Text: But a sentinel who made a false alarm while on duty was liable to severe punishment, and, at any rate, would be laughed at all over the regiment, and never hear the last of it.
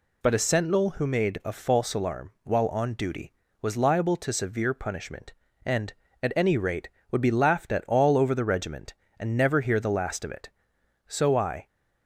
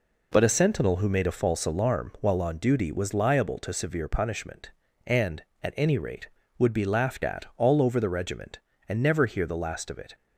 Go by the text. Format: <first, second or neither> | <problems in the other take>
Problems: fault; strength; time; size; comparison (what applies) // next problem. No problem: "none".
second | goes on to say "So I"; from 11.0 s on; 0.60 s long